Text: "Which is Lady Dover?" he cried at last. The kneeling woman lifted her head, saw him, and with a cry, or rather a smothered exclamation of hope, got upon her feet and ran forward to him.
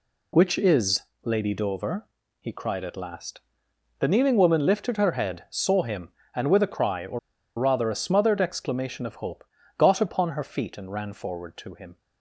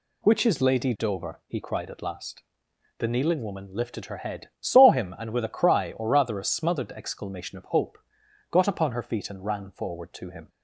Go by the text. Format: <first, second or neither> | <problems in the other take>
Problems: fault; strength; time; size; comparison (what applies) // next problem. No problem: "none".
second | pauses between "is" and "Lady"; slight; at 1.0 s; 0.20 s long // pauses between "or" and "rather"; at 7.1 s; 0.38 s long